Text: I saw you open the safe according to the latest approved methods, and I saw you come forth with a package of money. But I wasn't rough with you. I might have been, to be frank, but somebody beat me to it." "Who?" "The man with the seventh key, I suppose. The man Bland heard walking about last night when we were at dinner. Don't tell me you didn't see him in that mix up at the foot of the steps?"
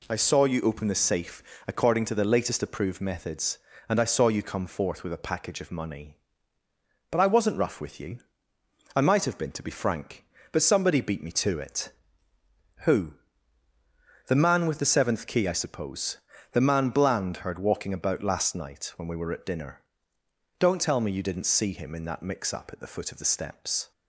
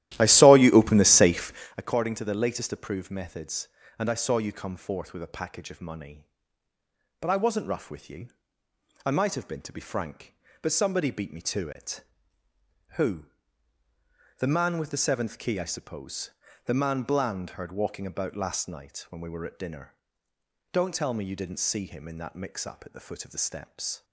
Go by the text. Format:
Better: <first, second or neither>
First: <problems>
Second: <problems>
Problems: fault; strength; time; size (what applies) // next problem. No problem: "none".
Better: first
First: pauses between "safe" and "according"; slight; at 1.4 s; 0.24 s long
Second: starts louder than the rest; strong; until 1.8 s; 14 dB // pauses between "safe" and "according"; slight; at 1.5 s; 0.24 s long